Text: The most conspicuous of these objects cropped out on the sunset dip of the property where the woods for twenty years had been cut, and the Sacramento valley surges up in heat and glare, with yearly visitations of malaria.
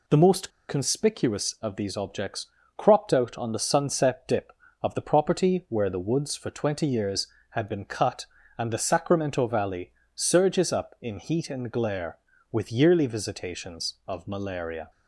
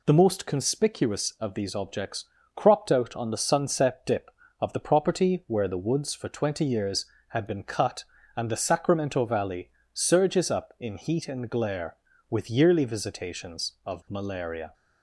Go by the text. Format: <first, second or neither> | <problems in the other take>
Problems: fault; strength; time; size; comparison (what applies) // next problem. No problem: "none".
second | pauses between "most" and "conspicuous"; slight; at 0.5 s; 0.18 s long // pauses between "objects" and "cropped"; slight; at 2.4 s; 0.32 s long; slight in the second // pauses between "valley" and "surges"; slight; at 9.9 s; 0.22 s long; slight in the second